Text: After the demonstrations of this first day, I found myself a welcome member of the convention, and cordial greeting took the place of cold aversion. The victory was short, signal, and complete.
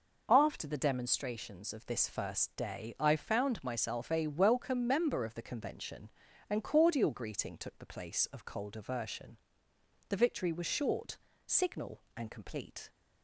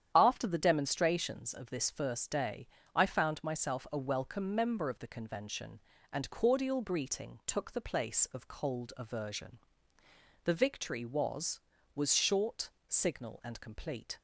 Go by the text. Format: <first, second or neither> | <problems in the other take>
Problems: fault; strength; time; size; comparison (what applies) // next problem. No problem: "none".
first | starts louder than the rest; strong; until 1.1 s; 9.5 dB // says "was" twice; at 11.9 s